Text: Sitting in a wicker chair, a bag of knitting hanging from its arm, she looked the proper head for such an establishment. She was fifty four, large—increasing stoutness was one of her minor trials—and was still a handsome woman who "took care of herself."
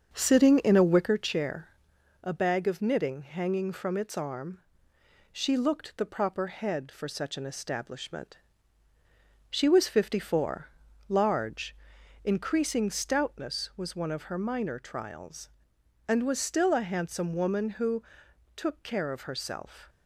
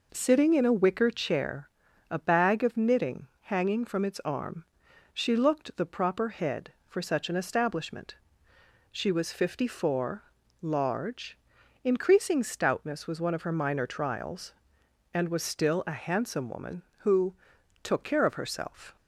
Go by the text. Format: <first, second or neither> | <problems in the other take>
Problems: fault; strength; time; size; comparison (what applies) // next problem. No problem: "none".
second | starts louder than the rest; until 1.1 s; 7 dB // pauses between "who" and "took"; noticeable; at 18.0 s; 0.52 s long; noticeable in the second